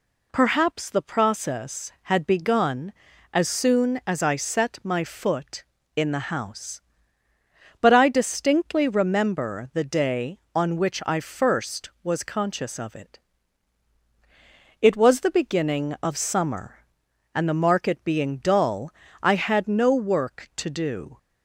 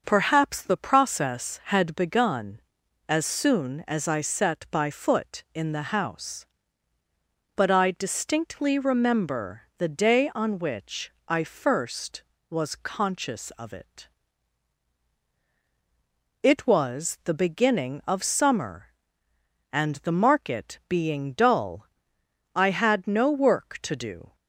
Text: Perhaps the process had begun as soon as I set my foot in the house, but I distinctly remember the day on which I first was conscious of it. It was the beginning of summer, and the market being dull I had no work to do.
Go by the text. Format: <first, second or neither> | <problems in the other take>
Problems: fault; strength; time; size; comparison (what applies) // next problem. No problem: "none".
first | starts louder than the rest; until 1.0 s; 6.5 dB // says "by" for "my"; at 4.7 s // pauses between "remember" and "the"; slight; at 9.6 s; 0.16 s long // pauses between "which" and "I"; slight; at 11.1 s; 0.16 s long // pauses between "dull" and "I"; noticeable; at 21.8 s; 0.68 s long; slight in the first